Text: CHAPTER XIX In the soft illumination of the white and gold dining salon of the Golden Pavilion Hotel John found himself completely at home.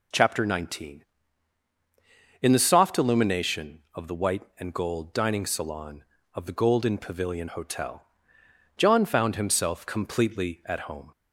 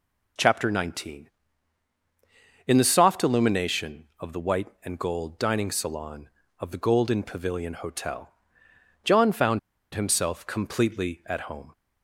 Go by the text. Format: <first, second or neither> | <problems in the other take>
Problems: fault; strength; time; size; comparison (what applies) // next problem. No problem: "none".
first | pauses between "Hotel" and "John"; noticeable; at 8.3 s; 0.72 s long; noticeable in the first // pauses between "found" and "himself"; slight; at 9.5 s; 0.34 s long